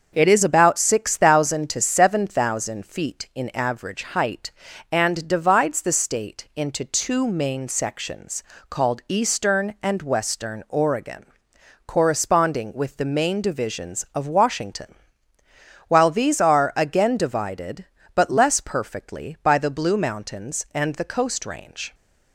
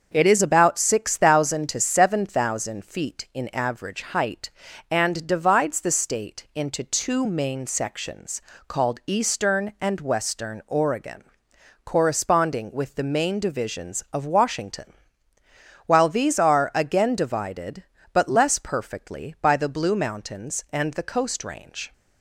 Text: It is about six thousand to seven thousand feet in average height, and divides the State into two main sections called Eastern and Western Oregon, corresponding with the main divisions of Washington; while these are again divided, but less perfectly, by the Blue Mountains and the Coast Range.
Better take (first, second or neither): neither